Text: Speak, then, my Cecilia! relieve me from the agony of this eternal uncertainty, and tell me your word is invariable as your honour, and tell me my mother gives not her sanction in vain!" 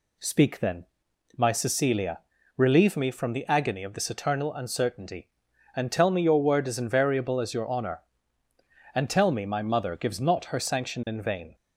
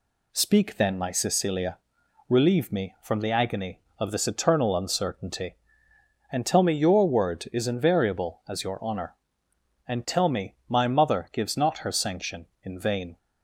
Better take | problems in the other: neither | none

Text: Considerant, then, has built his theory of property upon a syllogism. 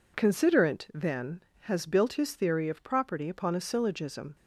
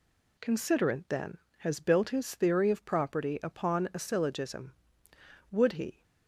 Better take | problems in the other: first | goes on to say "Would he"; from 5.5 s on; 0.52 s long

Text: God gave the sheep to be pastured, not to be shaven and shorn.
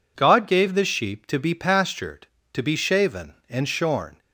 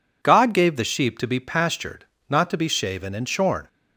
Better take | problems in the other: second | skips "not"; at 2.4 s

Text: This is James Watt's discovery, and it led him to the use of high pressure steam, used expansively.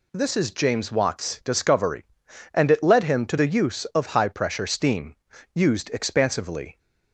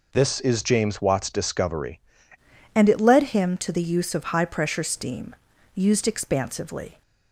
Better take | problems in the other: first | changes voice at "and"; from 2.7 s on; 4.3 s long

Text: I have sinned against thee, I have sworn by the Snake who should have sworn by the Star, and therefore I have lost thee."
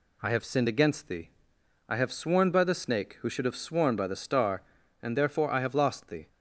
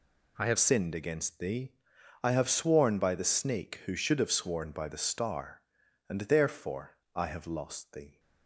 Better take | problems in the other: first | changes voice at "sinned"; from 0.5 s on; 7.6 s long // pauses between "therefore" and "I"; slight; at 6.9 s; 0.22 s long

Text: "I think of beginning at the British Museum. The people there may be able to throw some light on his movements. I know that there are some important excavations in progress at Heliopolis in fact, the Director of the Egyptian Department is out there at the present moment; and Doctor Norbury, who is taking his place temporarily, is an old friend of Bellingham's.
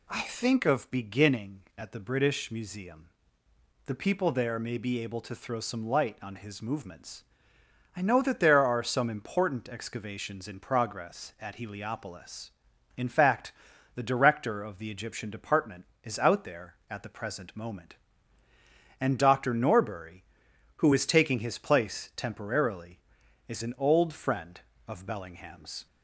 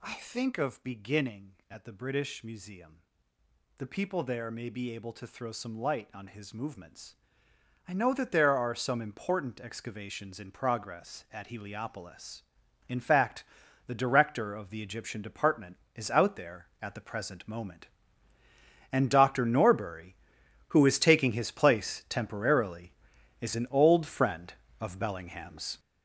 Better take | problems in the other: first | gets louder; strong; throughout; 8 dB

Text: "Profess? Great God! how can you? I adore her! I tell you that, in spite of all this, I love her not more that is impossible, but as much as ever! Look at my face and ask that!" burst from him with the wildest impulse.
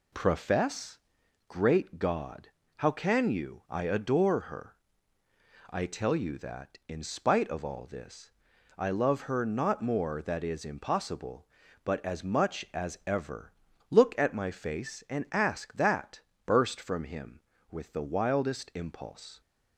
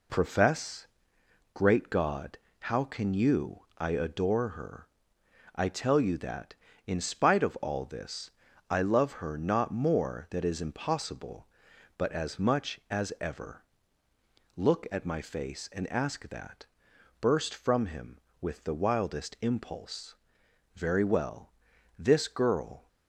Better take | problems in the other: first | goes on to say "Very well This girl"; strong; from 20.7 s on; 2.1 s long

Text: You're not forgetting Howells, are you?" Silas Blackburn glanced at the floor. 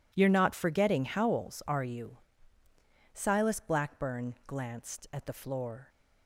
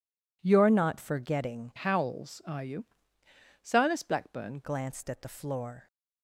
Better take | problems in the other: first | changes voice from "Howells" to "Blackburn"; from 1.7 to 4.6 s; 2.9 s long

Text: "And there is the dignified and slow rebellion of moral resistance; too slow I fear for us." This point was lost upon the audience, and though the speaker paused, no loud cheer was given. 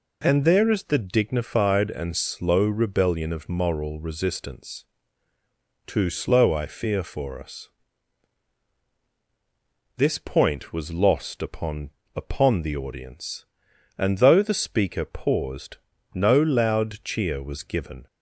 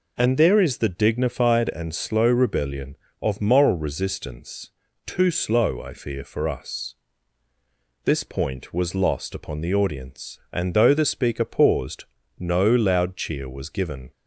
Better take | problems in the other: second | says "upon" twice; at 12.1 s

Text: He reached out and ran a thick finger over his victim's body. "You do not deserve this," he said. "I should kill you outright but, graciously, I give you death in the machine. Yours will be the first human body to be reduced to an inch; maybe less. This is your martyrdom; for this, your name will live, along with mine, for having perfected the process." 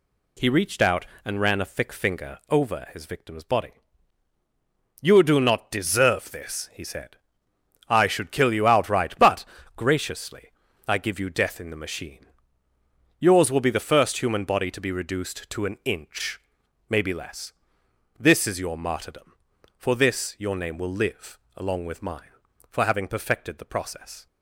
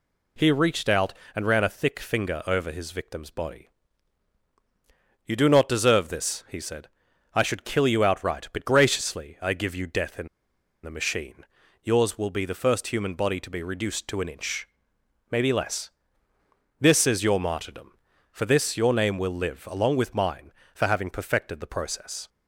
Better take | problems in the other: first | pauses between "in" and "the"; noticeable; at 10.2 s; 0.56 s long

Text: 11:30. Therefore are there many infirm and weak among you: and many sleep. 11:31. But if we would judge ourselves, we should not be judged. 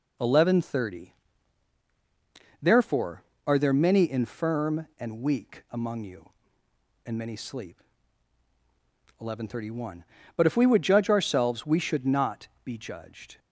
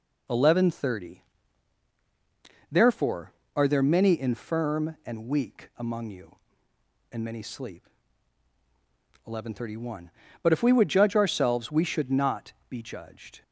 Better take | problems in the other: neither | pauses between "not" and "be"; slight; the same in both

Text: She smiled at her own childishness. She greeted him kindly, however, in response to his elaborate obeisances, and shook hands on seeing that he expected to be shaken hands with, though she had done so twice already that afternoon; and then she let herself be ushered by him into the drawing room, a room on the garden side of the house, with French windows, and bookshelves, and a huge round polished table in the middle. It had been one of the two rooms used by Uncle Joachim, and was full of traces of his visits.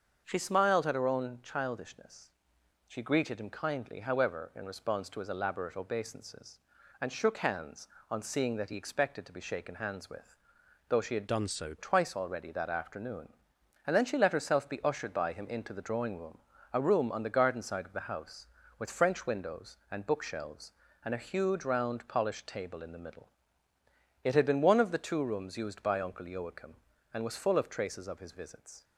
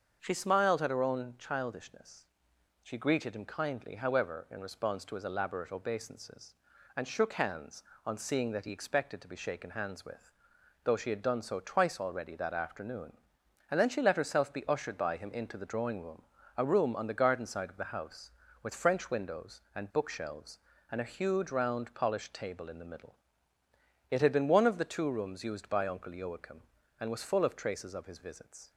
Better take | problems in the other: second | starts louder than the rest; until 1.2 s; 6.5 dB; also in the second // changes voice from "done" to "so"; from 11.2 to 11.7 s; 0.5 s long

